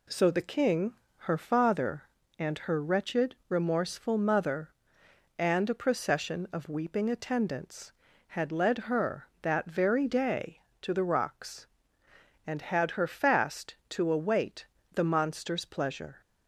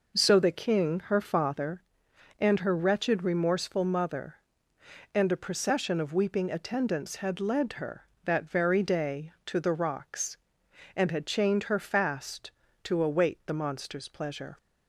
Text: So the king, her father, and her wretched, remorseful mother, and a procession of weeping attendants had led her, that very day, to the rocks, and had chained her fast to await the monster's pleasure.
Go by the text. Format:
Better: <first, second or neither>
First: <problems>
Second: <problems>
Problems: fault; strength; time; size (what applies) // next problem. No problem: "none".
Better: second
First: skips "chained"; at 12.9 s // pauses between "await" and "the"; slight; at 14.6 s; 0.30 s long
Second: none